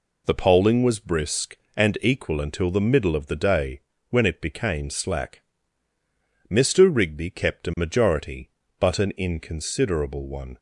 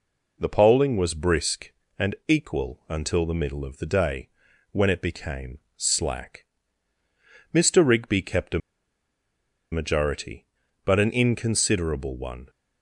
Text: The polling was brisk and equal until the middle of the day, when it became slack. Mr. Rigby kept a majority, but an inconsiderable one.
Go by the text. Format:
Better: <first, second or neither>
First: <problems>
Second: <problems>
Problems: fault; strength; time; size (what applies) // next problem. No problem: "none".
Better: first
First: none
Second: pauses between "became" and "slack"; slight; at 5.5 s; 0.18 s long // pauses between "a" and "majority"; at 8.5 s; 1.1 s long